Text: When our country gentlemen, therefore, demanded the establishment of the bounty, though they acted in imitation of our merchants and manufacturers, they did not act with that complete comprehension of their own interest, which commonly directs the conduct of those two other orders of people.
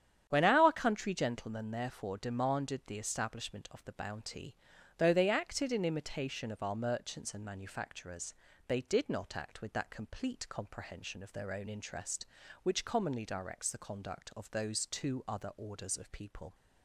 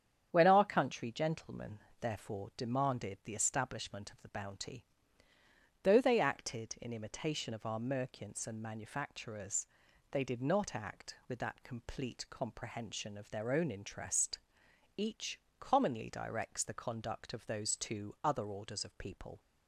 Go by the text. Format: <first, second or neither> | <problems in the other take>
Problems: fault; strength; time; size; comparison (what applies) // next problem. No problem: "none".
first | starts louder than the rest; strong; until 1.3 s; 9 dB; strong in the first // says "each" for "which"; at 14.9 s